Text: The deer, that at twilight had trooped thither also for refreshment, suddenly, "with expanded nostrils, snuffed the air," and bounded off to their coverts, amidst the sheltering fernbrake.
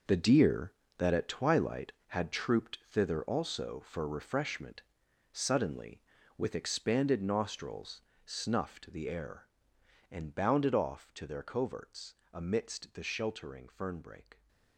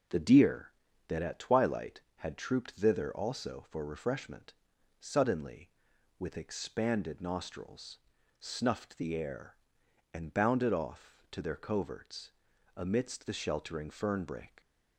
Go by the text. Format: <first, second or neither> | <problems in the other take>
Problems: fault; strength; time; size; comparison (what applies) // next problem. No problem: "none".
second | gets quieter; strong; throughout; 11 dB